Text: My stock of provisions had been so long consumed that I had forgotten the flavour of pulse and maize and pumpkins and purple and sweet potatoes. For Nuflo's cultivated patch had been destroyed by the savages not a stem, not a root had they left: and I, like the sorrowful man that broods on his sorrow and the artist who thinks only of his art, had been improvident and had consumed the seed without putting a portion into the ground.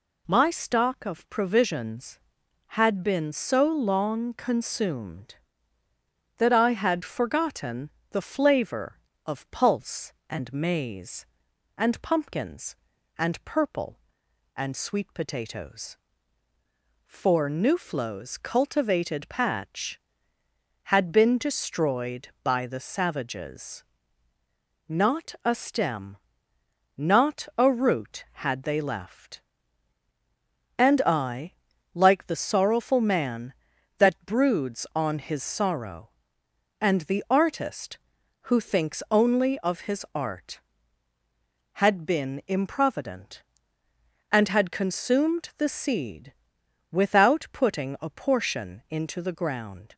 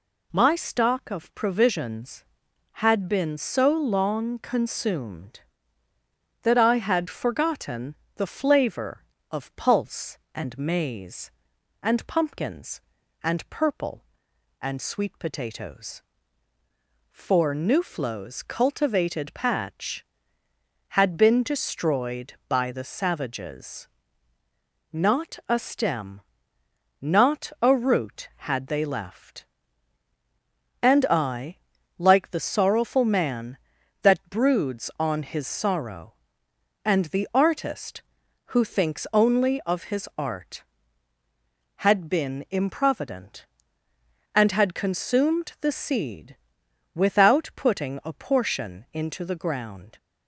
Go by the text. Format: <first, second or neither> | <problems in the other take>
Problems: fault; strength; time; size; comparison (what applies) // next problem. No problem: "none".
neither | pauses between "forgotten" and "the"; slight; the same in both // pauses between "savages" and "not"; the same in both // pauses between "seed" and "without"; noticeable; the same in both